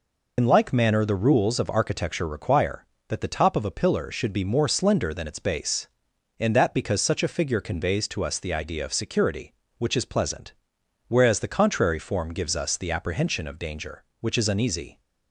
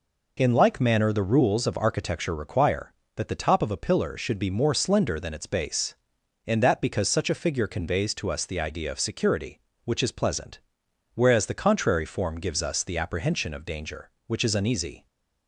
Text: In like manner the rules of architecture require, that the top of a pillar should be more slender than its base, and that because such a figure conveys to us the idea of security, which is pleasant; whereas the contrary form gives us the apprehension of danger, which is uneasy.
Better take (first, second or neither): second